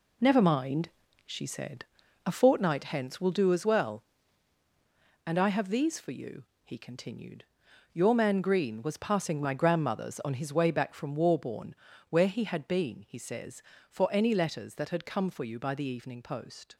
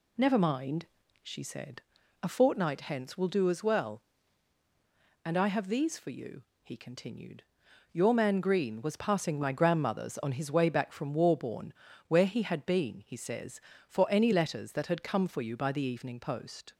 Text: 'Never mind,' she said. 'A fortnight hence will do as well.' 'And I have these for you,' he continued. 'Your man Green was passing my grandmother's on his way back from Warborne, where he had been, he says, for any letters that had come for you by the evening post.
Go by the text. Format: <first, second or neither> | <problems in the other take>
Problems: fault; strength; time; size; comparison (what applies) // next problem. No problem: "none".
second | gets quieter; strong; throughout; 7.5 dB